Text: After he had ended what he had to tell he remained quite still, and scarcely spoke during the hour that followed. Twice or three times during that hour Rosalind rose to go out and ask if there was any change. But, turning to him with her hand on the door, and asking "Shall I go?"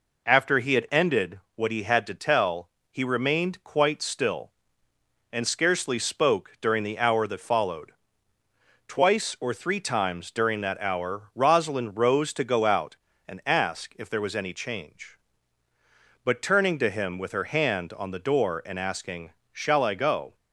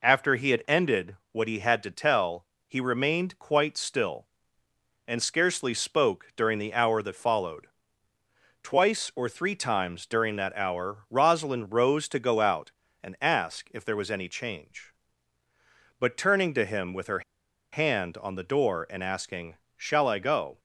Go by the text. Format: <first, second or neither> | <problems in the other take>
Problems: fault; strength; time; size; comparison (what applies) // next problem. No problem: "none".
first | pauses between "ended" and "what"; slight; at 1.1 s; 0.16 s long; slight in the first // pauses between "tell" and "he"; slight; at 2.4 s; 0.22 s long; slight in the first // pauses between "her" and "hand"; noticeable; at 17.2 s; 0.52 s long // pauses between "asking" and "Shall"; slight; at 19.5 s; 0.18 s long; slight in the first